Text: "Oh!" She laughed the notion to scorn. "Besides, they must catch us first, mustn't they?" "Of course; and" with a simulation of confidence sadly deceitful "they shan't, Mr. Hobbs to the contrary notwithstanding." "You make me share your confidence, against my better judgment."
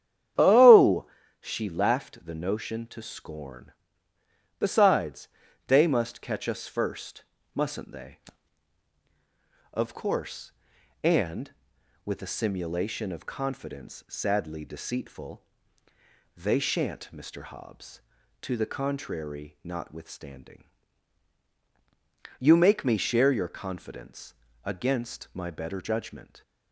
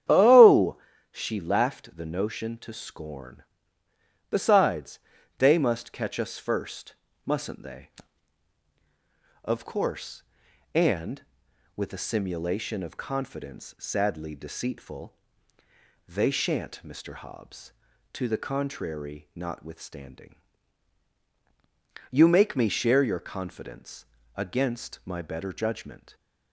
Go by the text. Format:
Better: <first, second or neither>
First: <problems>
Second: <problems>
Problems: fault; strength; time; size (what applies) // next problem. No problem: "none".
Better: neither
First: starts louder than the rest; strong; until 1.6 s; 9.5 dB // pauses between "deceitful" and "they"; noticeable; at 15.4 s; 0.94 s long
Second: starts louder than the rest; strong; until 1.4 s; 9.5 dB // pauses between "deceitful" and "they"; noticeable; at 15.1 s; 0.94 s long